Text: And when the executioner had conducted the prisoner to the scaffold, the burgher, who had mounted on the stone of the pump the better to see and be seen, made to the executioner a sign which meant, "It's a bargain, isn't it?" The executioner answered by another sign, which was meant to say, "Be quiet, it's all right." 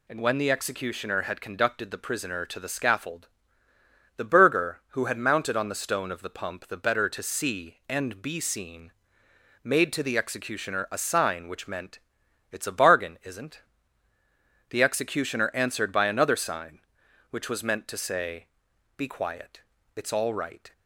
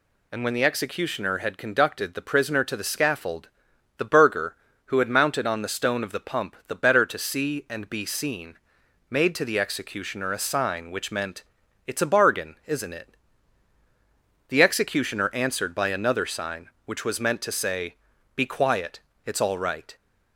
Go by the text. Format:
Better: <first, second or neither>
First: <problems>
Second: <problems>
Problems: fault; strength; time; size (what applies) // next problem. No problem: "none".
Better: second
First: skips "it"; at 14.1 s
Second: none